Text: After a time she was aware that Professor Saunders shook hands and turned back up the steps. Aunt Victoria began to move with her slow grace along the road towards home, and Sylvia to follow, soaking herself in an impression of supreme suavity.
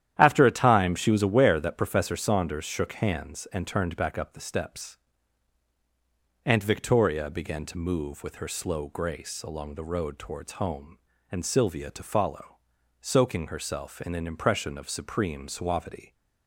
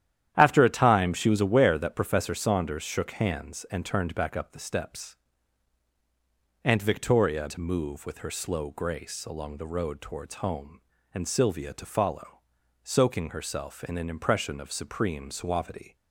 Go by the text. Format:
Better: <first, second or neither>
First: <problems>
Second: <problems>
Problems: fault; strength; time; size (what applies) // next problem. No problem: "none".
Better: first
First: starts louder than the rest; strong; until 1.1 s; 11 dB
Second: starts louder than the rest; strong; until 1.3 s; 11 dB // skips "began"; at 7.4 s